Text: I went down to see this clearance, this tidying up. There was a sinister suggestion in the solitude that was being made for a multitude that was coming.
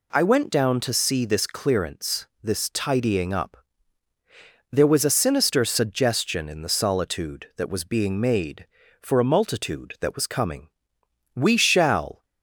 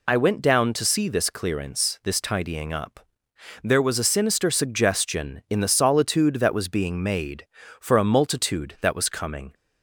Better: second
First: goes on to say "We shall"; noticeable; from 11.3 s on; 0.92 s long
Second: none

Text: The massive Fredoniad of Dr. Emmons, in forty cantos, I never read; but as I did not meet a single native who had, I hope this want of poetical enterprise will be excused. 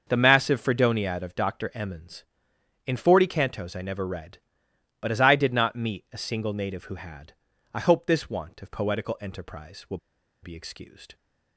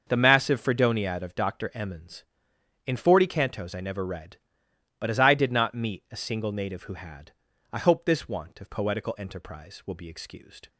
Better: second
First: starts louder than the rest; until 1.0 s; 6.5 dB // pauses between "will" and "be"; at 9.9 s; 0.44 s long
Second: starts louder than the rest; until 1.0 s; 6.5 dB

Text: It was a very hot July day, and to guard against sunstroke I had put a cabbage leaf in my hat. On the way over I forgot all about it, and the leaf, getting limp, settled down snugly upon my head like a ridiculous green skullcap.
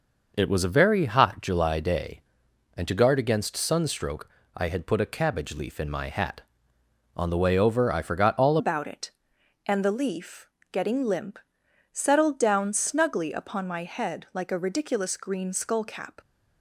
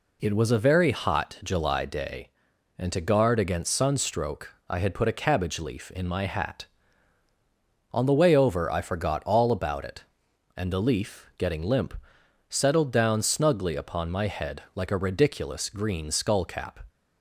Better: second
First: pauses between "sunstroke" and "I"; slight; at 4.2 s; 0.28 s long // changes voice at "about"; from 8.5 s on; 7.7 s long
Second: pauses between "sunstroke" and "I"; slight; at 4.5 s; 0.16 s long

